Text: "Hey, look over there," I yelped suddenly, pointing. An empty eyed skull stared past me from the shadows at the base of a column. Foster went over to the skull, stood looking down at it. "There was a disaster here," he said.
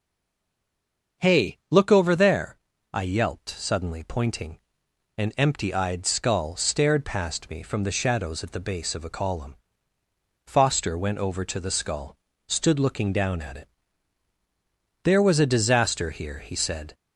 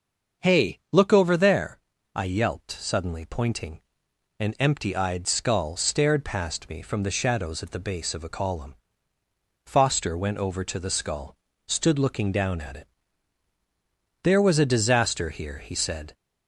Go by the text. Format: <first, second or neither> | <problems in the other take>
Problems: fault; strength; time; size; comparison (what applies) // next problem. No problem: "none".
second | stays silent before the first word; noticeable; until 1.2 s; 1.2 s long // starts louder than the rest; until 2.3 s; 6.5 dB; also in the second